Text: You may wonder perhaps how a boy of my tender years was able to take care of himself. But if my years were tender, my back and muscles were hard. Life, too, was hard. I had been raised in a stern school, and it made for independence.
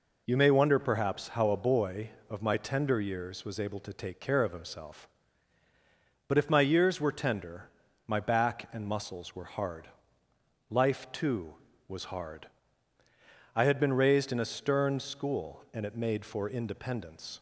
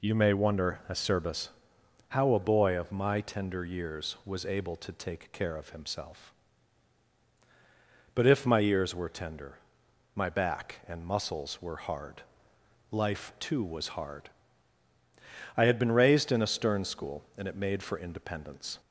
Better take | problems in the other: first | says "acerbus" for "perhaps"; at 0.8 s

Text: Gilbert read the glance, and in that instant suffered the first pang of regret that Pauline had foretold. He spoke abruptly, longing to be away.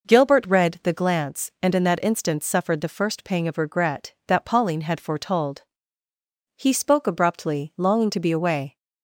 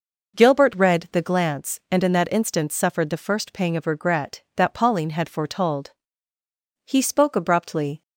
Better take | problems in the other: first | stops before "longing to be away"; at 8.0 s

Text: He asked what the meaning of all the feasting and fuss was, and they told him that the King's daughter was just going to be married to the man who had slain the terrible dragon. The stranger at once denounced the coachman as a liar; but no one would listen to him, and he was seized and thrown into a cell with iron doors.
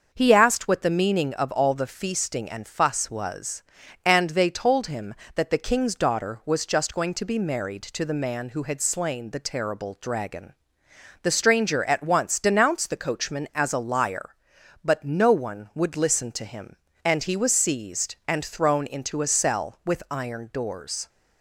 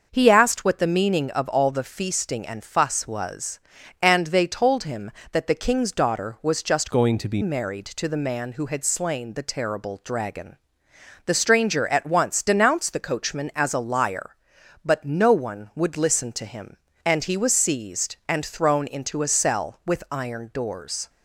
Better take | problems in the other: first | starts louder than the rest; noticeable; until 1.1 s; 6 dB; also in the first // changes voice from "going" to "be"; from 6.9 to 7.4 s; 0.5 s long

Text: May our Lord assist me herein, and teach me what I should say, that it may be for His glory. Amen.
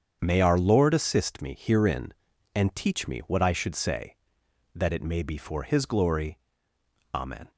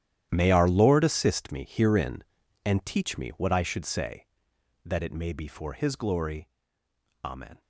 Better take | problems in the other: first | gets quieter; strong; throughout; 15.5 dB // starts louder than the rest; strong; until 1.3 s; 11.5 dB; strong in the first

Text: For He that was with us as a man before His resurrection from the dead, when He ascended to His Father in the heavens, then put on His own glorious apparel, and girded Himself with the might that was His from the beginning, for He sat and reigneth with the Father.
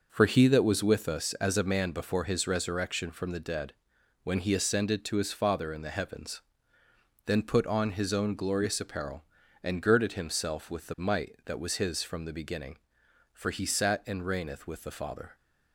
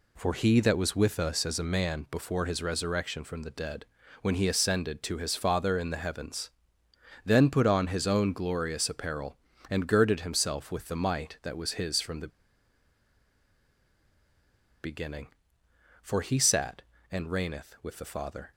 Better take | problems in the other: first | pauses between "the" and "beginning"; strong; at 12.2 s; 2.5 s long

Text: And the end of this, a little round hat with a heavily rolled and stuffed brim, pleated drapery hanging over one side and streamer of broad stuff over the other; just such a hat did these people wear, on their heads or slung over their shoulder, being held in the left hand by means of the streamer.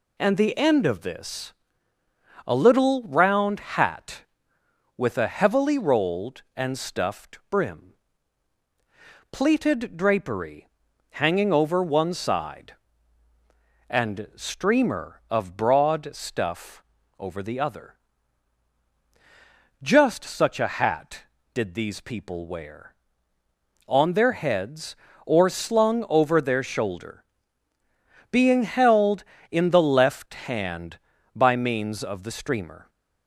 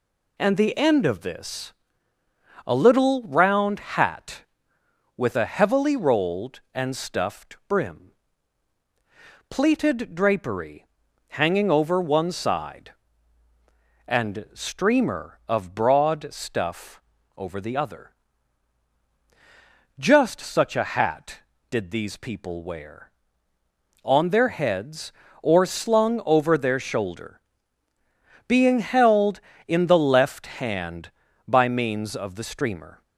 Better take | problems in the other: neither | pauses between "drapery" and "hanging"; the same in both // pauses between "stuff" and "over"; the same in both

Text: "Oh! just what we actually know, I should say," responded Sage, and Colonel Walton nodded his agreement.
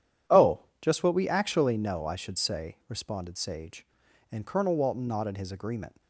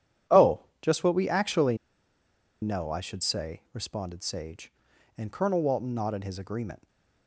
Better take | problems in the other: first | pauses between "actually" and "know"; noticeable; at 1.7 s; 0.84 s long // stays silent after the last word; slight; from 6.7 s on; 0.5 s long

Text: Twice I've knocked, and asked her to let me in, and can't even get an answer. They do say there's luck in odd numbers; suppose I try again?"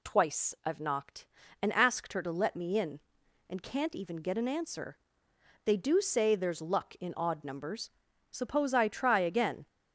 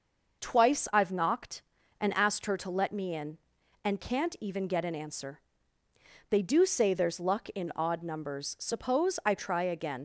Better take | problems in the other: first | leaves "again" unfinished; at 9.9 s; 75 ms

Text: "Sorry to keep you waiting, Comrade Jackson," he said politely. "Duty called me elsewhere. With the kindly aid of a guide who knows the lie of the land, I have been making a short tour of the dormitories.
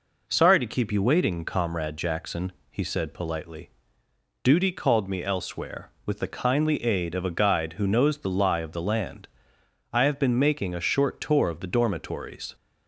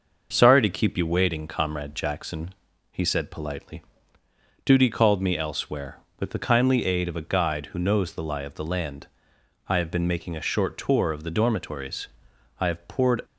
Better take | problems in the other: first | starts louder than the rest; noticeable; until 1.3 s; 6 dB // goes on to say "I have poured"; noticeable; from 12.6 s on; 0.62 s long

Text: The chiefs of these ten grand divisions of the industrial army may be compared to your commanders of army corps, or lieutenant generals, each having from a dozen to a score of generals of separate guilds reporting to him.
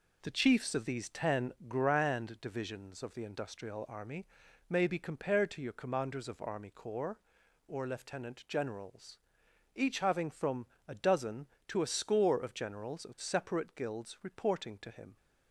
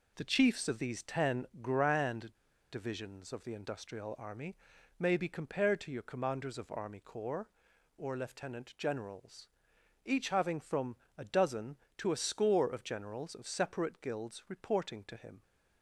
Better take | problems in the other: first | pauses between "ten" and "grand"; slight; at 1.4 s; 0.16 s long; slight in the first // pauses between "grand" and "divisions"; at 2.3 s; 0.38 s long // pauses between "army" and "may"; at 4.5 s; 0.42 s long; also in the first // pauses between "from" and "a"; slight; at 10.9 s; 0.22 s long; slight in the first

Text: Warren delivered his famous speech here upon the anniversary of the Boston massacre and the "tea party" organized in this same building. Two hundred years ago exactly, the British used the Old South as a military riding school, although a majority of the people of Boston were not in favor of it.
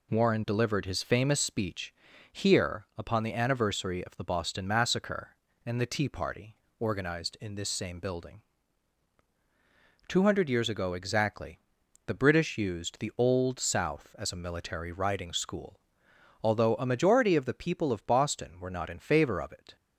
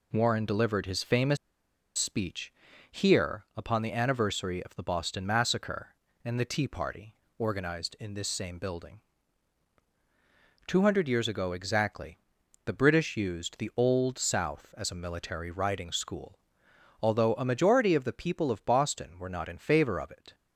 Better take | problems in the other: first | pauses between "famous" and "speech"; noticeable; at 1.3 s; 0.61 s long // pauses between "speech" and "here"; at 2.5 s; 0.38 s long; also in the first // pauses between "party" and "organized"; slight; at 7.1 s; 0.22 s long; slight in the first

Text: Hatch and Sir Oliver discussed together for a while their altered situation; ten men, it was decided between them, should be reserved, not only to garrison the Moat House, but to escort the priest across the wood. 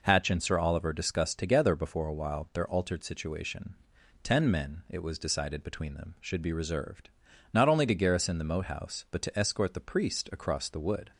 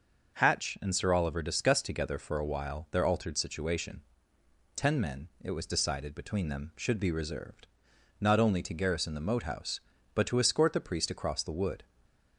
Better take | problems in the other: second | says "before" for "for"; at 1.7 s

